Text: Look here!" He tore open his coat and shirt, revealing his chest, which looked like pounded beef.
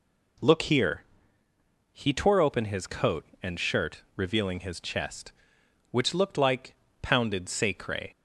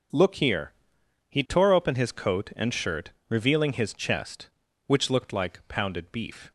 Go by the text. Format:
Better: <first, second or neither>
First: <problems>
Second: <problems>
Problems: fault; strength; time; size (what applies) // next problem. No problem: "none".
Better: second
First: pauses between "like" and "pounded"; slight; at 6.7 s; 0.26 s long // says "sacre" for "beef"; at 7.4 s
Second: none